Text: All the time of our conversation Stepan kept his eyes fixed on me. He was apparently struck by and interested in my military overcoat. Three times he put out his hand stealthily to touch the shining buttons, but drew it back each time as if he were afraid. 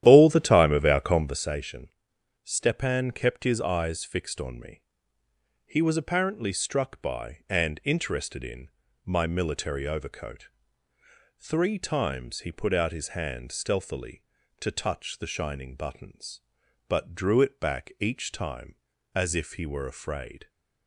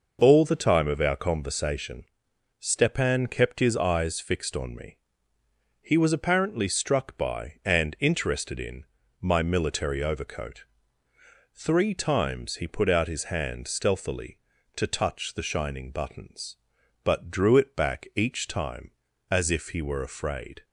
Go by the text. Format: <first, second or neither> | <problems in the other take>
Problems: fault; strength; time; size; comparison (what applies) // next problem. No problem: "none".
second | starts louder than the rest; strong; until 1.5 s; 11.5 dB // pauses between "conversation" and "Stepan"; noticeable; at 1.8 s; 0.54 s long; noticeable in the second // pauses between "in" and "my"; at 8.6 s; 0.38 s long; also in the second